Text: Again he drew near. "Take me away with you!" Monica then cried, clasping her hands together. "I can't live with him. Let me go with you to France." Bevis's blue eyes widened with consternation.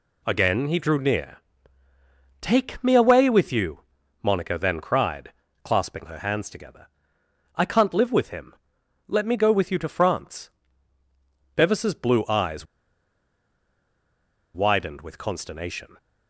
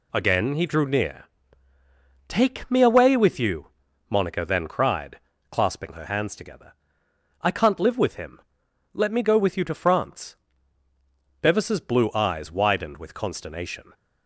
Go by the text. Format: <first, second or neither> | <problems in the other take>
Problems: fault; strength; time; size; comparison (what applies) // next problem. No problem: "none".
second | pauses between "eyes" and "widened"; strong; at 12.6 s; 1.8 s long